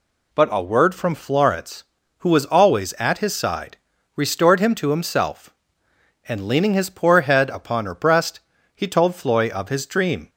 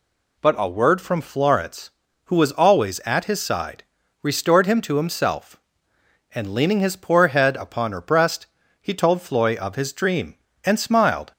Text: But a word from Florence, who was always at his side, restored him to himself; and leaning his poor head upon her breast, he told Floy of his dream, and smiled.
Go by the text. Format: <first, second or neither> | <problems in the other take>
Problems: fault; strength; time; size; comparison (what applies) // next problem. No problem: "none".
second | stops before "and smiled"; at 10.2 s